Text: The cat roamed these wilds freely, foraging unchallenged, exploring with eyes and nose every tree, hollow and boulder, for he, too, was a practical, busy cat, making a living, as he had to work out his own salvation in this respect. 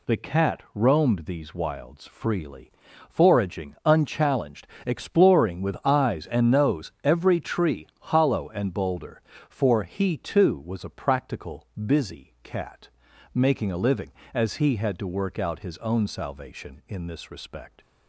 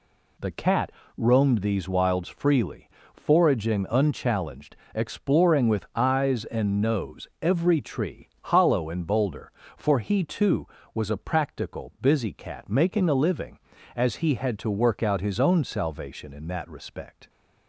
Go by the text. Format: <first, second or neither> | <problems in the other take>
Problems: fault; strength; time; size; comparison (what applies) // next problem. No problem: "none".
first | pauses between "cat" and "roamed"; slight; at 0.9 s; 0.26 s long // says "that" for "this"; at 16.4 s